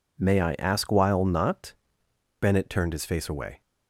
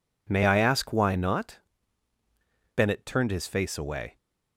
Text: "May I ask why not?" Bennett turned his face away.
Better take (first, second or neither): second